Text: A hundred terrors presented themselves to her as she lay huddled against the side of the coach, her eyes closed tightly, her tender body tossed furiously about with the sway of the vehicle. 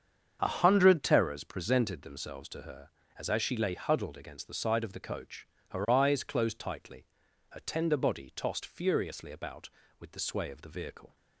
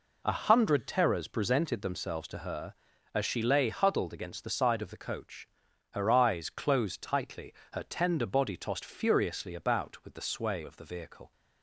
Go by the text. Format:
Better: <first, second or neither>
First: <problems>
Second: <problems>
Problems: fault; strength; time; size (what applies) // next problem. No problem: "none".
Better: second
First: starts louder than the rest; strong; until 1.4 s; 7.5 dB // says "as" twice; at 3.2 s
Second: none